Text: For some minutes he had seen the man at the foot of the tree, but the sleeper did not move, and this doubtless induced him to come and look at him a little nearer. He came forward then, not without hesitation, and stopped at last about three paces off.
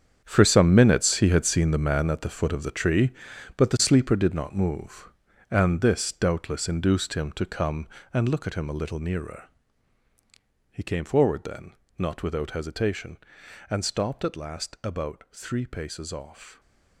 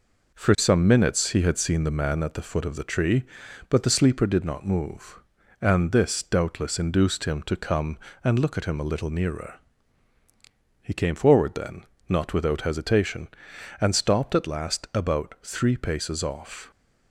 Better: second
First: gets quieter; strong; throughout; 12.5 dB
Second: none

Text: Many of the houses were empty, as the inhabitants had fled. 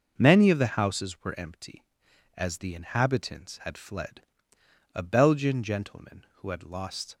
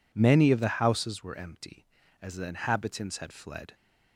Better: second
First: goes on to say "A Belgian gentleman who had lost"; strong; from 4.9 s on; 2.2 s long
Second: none

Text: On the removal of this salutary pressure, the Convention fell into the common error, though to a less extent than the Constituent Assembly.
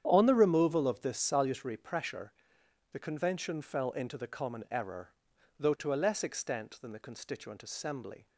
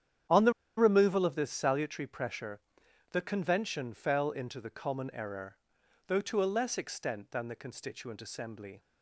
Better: first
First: starts louder than the rest; strong; until 1.0 s; 9 dB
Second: starts louder than the rest; strong; until 1.5 s; 9.5 dB // pauses between "the" and "removal"; slight; at 0.5 s; 0.25 s long

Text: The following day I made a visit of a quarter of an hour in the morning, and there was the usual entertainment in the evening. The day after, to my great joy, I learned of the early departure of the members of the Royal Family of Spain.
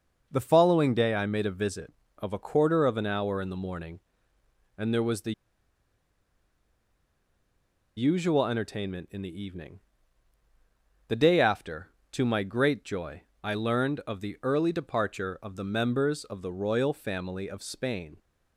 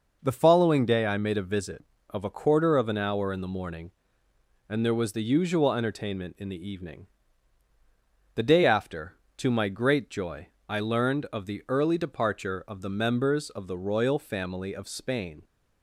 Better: second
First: pauses between "the" and "usual"; strong; at 5.3 s; 2.6 s long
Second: none

